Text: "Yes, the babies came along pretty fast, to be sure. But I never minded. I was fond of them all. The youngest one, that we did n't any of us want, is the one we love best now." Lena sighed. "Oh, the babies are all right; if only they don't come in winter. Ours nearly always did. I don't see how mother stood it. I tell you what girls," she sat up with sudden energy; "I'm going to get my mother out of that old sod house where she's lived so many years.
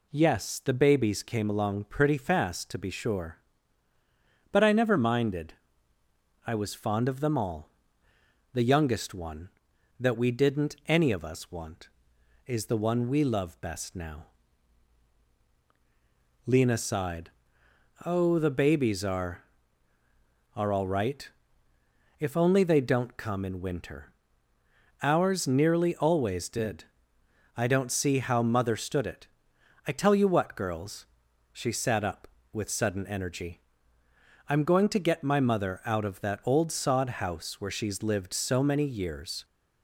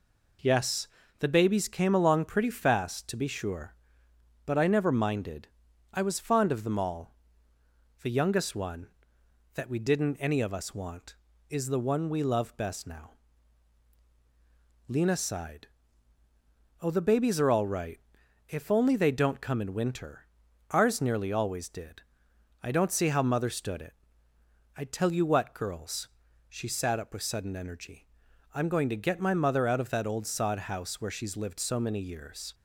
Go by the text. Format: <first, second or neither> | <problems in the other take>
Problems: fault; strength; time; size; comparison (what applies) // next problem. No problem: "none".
second | says "are" twice; at 20.5 s